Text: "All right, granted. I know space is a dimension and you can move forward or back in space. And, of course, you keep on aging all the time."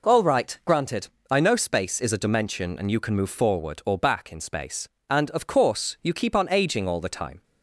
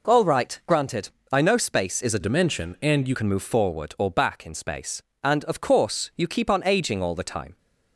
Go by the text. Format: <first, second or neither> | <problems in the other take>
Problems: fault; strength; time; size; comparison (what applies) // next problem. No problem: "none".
first | changes voice from "dimension" to "you"; from 2.2 to 3.1 s; 0.9 s long